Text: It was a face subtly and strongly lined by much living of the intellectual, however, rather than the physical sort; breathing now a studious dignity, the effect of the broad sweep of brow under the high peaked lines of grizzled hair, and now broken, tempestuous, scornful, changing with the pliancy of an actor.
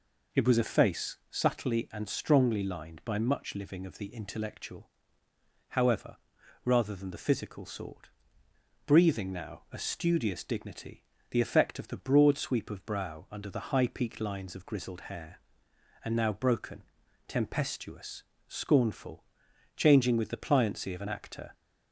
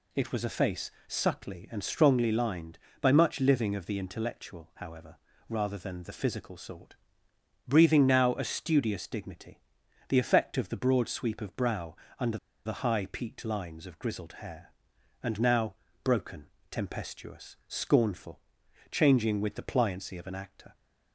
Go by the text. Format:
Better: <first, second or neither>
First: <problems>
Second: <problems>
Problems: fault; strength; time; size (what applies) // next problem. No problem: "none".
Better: first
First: none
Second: pauses between "face" and "subtly"; slight; at 0.9 s; 0.16 s long // pauses between "brow" and "under"; slight; at 11.9 s; 0.24 s long // pauses between "under" and "the"; slight; at 12.3 s; 0.28 s long // pauses between "now" and "broken"; slight; at 15.7 s; 0.30 s long